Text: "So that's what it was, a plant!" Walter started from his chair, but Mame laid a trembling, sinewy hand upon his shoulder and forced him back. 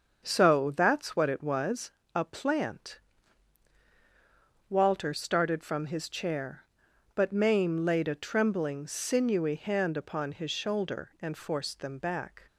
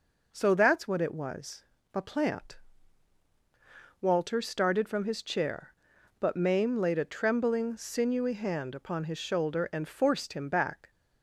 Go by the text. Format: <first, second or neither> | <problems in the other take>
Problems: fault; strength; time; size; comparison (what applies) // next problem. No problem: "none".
second | starts louder than the rest; until 1.2 s; 6.5 dB // says "them" for "him"; at 11.8 s